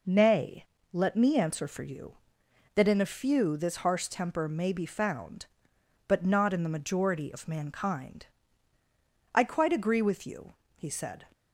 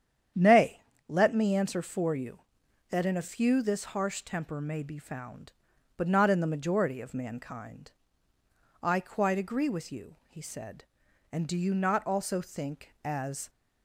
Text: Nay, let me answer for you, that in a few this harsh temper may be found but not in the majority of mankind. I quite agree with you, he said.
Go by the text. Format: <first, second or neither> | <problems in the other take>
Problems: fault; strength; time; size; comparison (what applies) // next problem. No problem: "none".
first | starts louder than the rest; strong; until 1.6 s; 9 dB // goes on to say "And do you not also think as"; strong; from 11.2 s on; 2.2 s long